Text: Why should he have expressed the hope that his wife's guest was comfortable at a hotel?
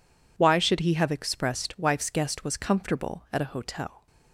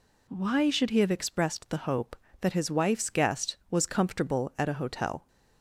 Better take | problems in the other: second | skips "the hope that his"; at 1.7 s

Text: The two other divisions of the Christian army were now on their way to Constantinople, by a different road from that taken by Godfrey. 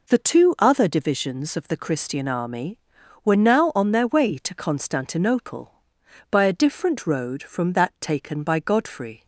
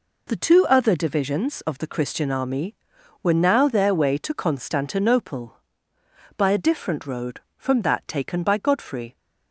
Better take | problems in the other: first | skips "on"; at 3.6 s

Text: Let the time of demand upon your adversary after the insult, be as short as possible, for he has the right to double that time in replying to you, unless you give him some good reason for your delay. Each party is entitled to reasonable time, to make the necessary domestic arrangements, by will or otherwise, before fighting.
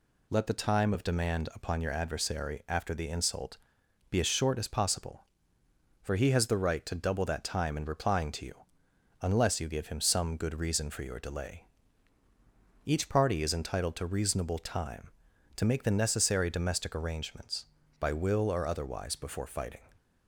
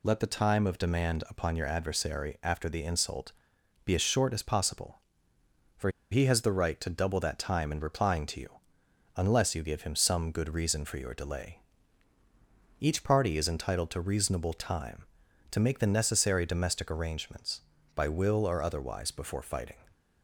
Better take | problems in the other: first | pauses between "for" and "he"; slight; at 5.9 s; 0.21 s long

